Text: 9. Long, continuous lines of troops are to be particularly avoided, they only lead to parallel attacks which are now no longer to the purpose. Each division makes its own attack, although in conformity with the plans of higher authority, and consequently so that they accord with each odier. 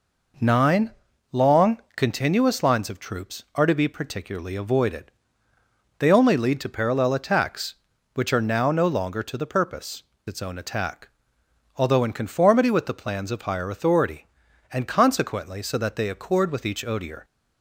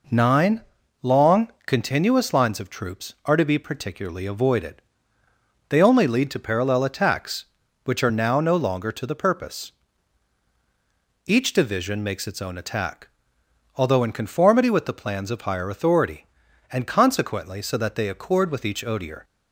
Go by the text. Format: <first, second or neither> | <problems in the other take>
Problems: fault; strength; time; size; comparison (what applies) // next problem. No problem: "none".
second | skips "Each division makes"; at 10.1 s